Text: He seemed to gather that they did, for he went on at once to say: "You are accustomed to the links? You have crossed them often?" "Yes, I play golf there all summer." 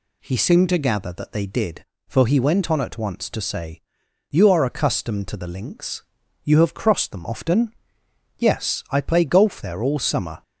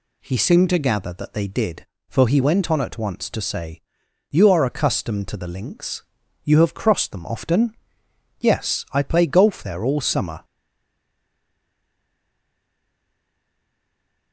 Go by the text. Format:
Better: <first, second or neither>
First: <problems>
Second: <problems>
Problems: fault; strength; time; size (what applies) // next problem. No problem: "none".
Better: first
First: none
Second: stays silent after the last word; strong; from 10.4 s on; 3.9 s long